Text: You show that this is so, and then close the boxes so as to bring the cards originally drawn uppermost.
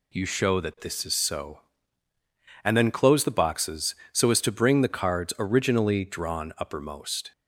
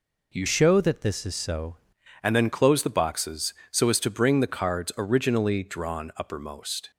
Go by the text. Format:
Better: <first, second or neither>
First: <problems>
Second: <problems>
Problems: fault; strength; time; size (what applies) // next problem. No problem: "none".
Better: first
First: none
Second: changes voice from "show" to "so"; from 0.4 to 1.7 s; 1.3 s long